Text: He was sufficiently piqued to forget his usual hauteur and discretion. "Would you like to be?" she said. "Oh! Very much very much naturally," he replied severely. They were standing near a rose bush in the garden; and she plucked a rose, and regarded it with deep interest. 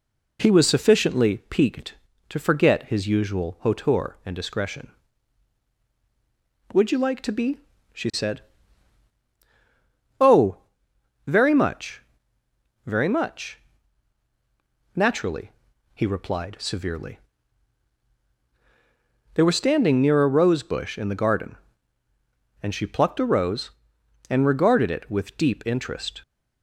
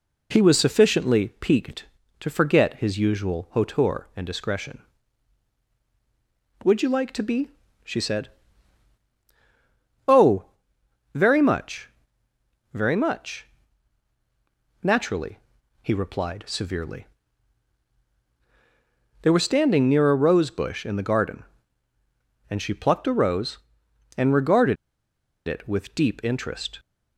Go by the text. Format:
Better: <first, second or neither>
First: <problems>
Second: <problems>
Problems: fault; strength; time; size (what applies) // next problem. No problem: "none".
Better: first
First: pauses between "much" and "very"; noticeable; at 12.0 s; 0.82 s long // pauses between "much" and "naturally"; strong; at 13.5 s; 1.3 s long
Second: pauses between "much" and "very"; noticeable; at 11.8 s; 0.82 s long // pauses between "much" and "naturally"; strong; at 13.4 s; 1.3 s long // pauses between "regarded" and "it"; noticeable; at 24.7 s; 0.71 s long